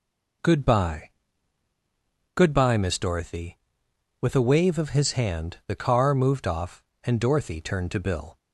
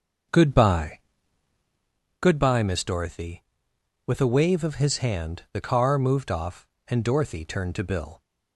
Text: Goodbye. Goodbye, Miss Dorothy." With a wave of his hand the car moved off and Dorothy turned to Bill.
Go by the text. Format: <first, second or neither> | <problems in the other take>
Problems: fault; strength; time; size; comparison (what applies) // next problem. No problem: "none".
first | starts louder than the rest; until 1.9 s; 6.5 dB